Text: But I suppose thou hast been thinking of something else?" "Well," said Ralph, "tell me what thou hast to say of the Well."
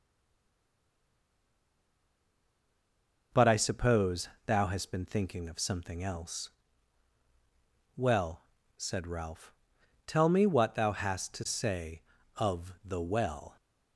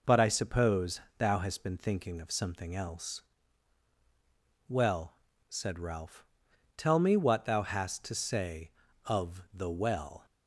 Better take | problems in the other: second | stays silent before the first word; strong; until 3.3 s; 3.3 s long // pauses between "suppose" and "thou"; slight; at 4.2 s; 0.16 s long; slight in the second

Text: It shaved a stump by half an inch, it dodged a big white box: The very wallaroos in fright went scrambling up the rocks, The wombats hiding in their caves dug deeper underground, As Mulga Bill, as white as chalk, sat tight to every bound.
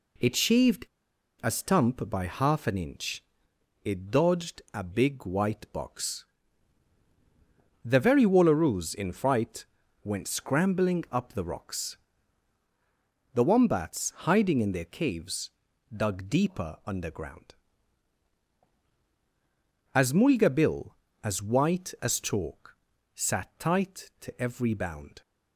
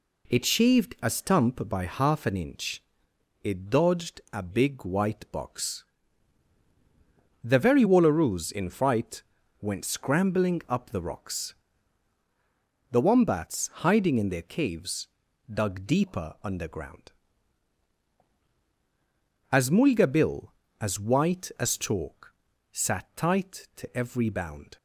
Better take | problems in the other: second | pauses between "shaved" and "a"; noticeable; at 0.8 s; 0.56 s long // pauses between "fright" and "went"; at 9.6 s; 0.38 s long; also in the second // pauses between "caves" and "dug"; at 15.5 s; 0.44 s long; also in the second

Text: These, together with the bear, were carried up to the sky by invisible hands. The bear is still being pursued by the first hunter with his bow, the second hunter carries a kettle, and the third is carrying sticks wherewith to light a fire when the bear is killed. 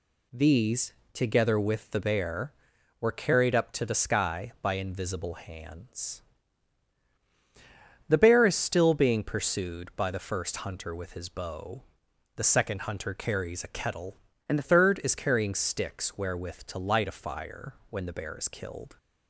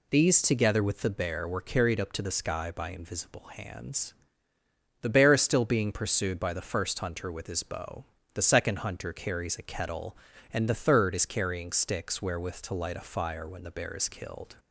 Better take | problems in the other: second | changes voice from "and" to "the"; from 14.4 to 14.6 s; 0.2 s long // pauses between "fire" and "when"; slight; at 17.7 s; 0.16 s long

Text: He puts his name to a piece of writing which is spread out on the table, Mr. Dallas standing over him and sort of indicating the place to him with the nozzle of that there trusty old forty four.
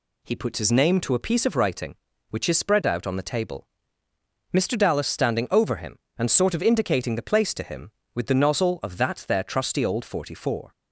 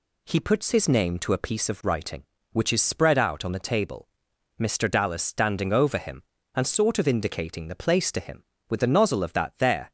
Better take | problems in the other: first | stops before "trusty old forty four"; at 9.8 s

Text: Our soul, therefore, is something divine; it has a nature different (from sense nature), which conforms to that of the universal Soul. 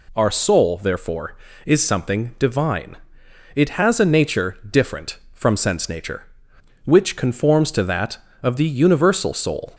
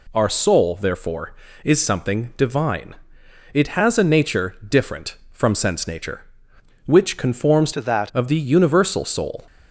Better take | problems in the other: first | changes voice from "to" to "that"; from 7.7 to 8.1 s; 0.4 s long

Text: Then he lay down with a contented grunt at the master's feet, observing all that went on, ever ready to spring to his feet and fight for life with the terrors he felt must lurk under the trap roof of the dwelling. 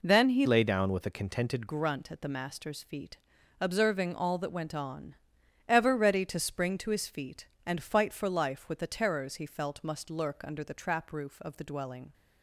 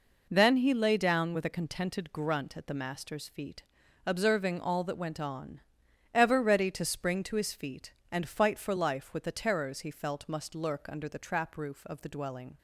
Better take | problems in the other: second | changes voice from "lay" to "contented"; from 0.4 to 1.6 s; 1.2 s long

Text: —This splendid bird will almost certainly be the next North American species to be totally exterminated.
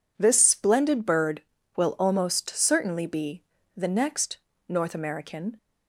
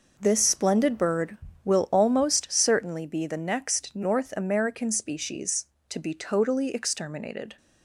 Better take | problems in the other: second | pauses between "be" and "the"; slight; at 3.4 s; 0.34 s long // pauses between "next" and "North"; slight; at 4.3 s; 0.32 s long // stops before "species to be totally exterminated"; at 5.5 s

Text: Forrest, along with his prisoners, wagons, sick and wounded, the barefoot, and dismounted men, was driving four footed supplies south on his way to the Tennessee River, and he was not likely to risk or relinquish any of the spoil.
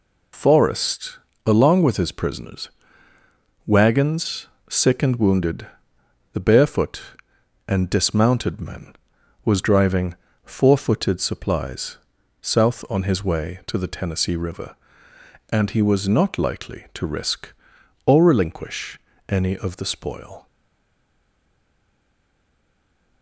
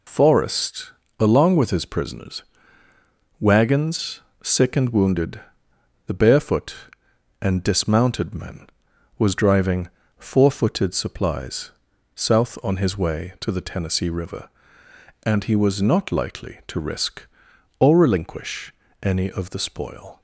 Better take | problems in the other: second | pauses between "driving" and "four"; slight; at 10.1 s; 0.28 s long; slight in the second // pauses between "supplies" and "south"; noticeable; at 11.9 s; 0.46 s long; noticeable in the second // pauses between "relinquish" and "any"; slight; at 18.9 s; 0.32 s long; slight in the second // stays silent after the last word; strong; from 20.4 s on; 2.8 s long

